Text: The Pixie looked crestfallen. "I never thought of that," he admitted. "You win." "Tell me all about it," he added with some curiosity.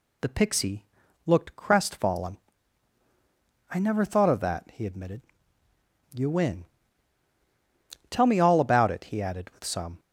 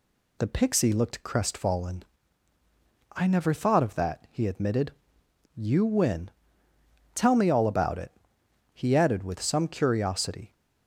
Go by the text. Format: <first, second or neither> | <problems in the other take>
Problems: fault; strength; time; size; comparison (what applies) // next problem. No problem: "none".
second | pauses between "Pixie" and "looked"; at 0.8 s; 0.42 s long // stops before "curiosity"; at 9.9 s